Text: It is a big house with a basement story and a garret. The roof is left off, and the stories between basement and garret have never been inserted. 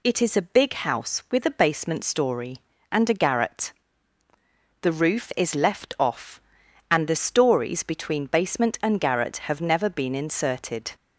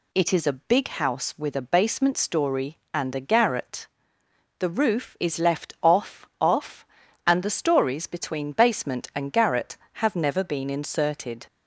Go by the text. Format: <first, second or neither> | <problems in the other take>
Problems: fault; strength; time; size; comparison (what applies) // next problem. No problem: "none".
first | says "off" twice; at 6.4 s